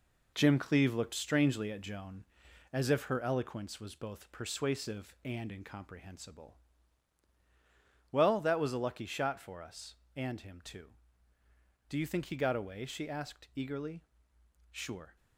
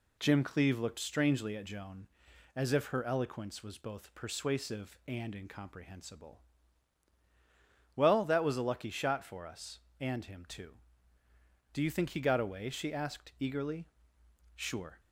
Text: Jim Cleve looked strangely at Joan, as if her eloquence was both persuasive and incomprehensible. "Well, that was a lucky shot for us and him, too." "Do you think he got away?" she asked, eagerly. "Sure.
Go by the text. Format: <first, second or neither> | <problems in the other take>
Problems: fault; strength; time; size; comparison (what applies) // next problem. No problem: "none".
second | gets quieter; throughout; 6.5 dB